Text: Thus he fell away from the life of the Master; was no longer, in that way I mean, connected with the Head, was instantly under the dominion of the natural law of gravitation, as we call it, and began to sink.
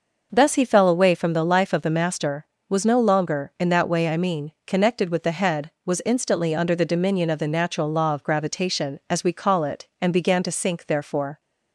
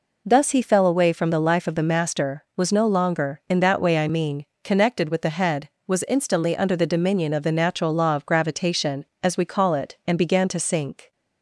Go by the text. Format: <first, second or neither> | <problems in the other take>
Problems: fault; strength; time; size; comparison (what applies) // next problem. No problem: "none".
second | goes on to say "Therefore"; from 10.8 s on; 0.54 s long